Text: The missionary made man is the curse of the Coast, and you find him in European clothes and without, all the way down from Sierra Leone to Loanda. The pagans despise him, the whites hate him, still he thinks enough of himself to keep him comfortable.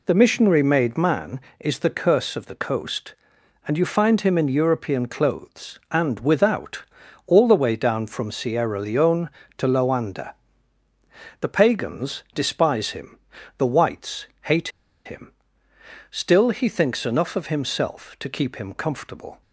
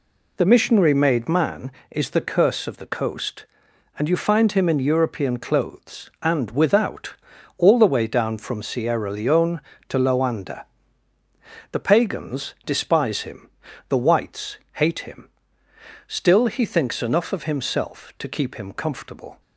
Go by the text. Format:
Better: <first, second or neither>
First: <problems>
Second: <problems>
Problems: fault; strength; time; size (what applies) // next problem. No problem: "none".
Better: second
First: pauses between "whites" and "hate"; slight; at 14.2 s; 0.16 s long // pauses between "hate" and "him"; at 14.6 s; 0.36 s long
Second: pauses between "whites" and "hate"; slight; at 14.5 s; 0.16 s long